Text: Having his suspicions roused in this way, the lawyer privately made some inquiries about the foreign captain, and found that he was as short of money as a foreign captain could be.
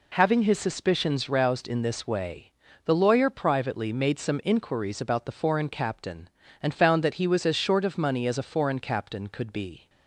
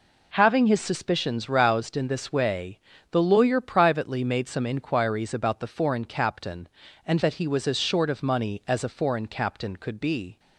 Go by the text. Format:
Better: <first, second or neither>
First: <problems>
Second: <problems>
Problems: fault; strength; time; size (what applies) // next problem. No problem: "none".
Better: first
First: none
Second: skips "found"; at 7.2 s